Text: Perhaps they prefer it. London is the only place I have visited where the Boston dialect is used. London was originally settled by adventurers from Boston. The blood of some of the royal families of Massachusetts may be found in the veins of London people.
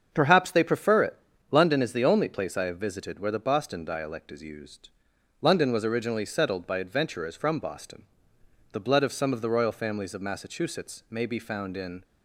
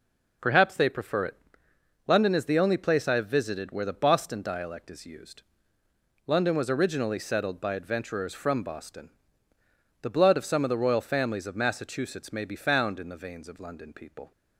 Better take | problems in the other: second | starts louder than the rest; until 1.1 s; 7 dB // stops before "the veins of London people"; at 12.0 s

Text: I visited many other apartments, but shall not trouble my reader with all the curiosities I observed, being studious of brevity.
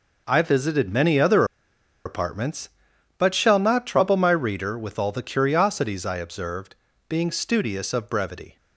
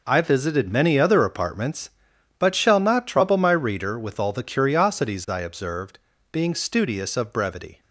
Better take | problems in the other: second | pauses between "other" and "apartments"; noticeable; at 1.4 s; 0.61 s long

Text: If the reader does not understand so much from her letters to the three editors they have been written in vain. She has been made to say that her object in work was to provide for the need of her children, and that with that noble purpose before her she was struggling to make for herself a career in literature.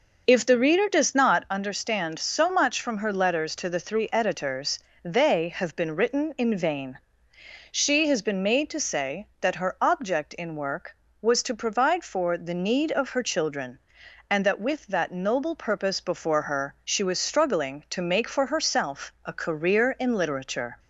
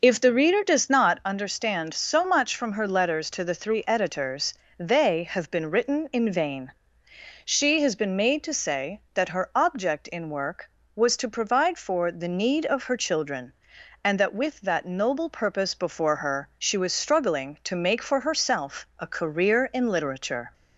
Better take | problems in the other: neither | pauses between "editors" and "they"; slight; the same in both

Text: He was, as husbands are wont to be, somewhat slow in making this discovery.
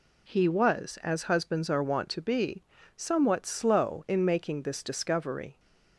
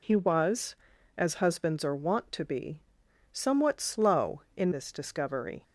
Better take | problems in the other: first | skips "making"; at 4.7 s

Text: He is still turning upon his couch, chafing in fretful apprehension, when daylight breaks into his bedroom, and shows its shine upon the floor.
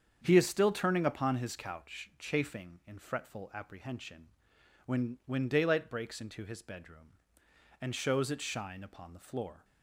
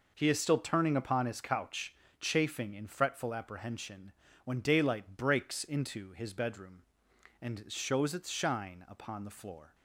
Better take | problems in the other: second | starts louder than the rest; strong; until 1.2 s; 7.5 dB // says "when" twice; at 5.2 s

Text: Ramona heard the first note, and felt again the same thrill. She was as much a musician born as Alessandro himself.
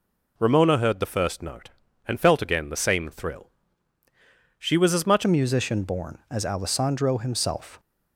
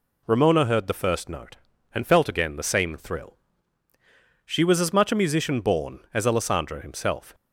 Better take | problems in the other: second | changes voice at "a"; from 5.2 s on; 2.5 s long

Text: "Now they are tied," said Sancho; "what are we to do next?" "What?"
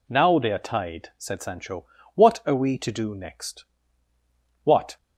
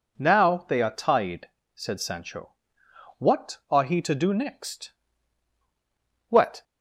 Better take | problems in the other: first | says "he" for "we"; at 3.8 s

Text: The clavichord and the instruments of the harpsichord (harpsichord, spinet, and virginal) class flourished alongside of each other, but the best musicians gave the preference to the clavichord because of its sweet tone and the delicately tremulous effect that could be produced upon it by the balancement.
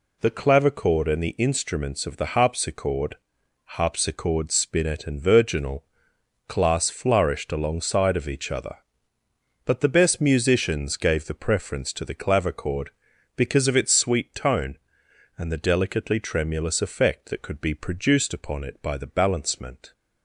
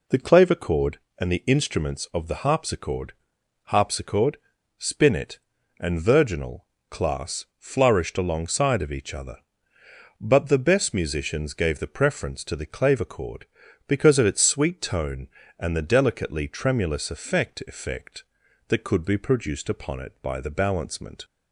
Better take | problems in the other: first | says "effect" twice; at 17.6 s

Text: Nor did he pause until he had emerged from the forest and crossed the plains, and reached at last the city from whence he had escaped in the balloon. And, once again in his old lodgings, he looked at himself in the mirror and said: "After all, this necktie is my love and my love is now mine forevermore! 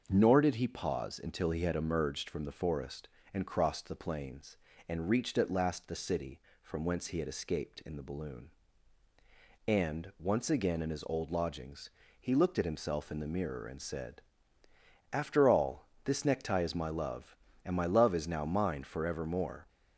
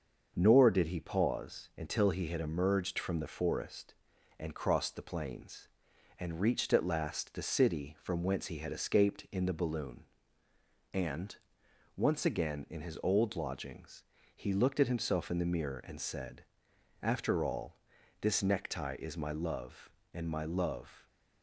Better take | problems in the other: first | starts louder than the rest; until 1.3 s; 6.5 dB; also in the first // stops before "is now mine forevermore"; at 21.0 s

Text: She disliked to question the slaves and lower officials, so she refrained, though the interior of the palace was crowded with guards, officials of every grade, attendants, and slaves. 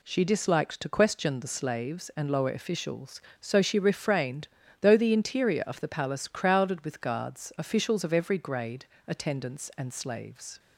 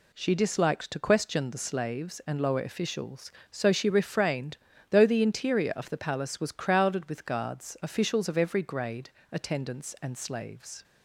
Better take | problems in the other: second | skips "was"; at 6.2 s

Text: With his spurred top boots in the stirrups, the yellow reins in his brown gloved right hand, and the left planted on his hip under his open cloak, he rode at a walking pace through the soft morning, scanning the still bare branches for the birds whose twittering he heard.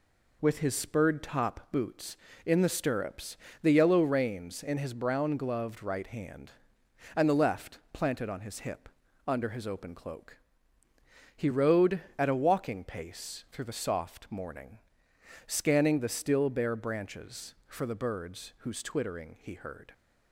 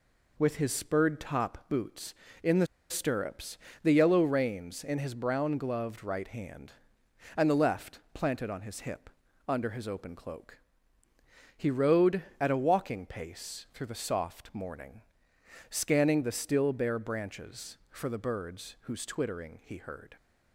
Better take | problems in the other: first | pauses between "the" and "stirrups"; slight; at 2.6 s; 0.23 s long // pauses between "hip" and "under"; at 9.0 s; 0.40 s long; also in the first

